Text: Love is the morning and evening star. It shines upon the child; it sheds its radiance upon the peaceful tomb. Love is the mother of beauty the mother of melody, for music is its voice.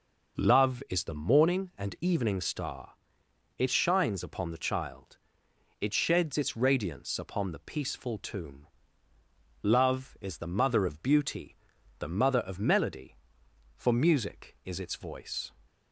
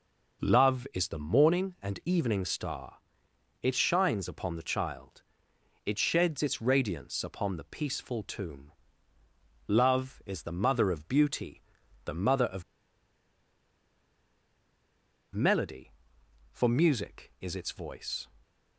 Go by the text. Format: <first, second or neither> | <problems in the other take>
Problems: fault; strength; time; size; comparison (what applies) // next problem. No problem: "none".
first | pauses between "beauty" and "the"; noticeable; at 11.6 s; 0.46 s long; noticeable in the first // pauses between "of" and "melody"; strong; at 12.6 s; 2.7 s long